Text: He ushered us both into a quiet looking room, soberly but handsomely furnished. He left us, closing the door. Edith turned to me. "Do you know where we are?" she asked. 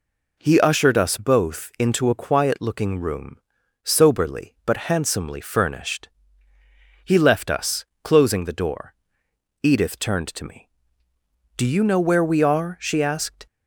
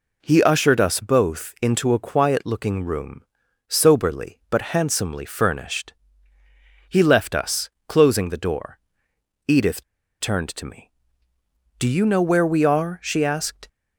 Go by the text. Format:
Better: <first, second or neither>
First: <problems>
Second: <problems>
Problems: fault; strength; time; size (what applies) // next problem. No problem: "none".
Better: first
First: none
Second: pauses between "Edith" and "turned"; at 9.8 s; 0.37 s long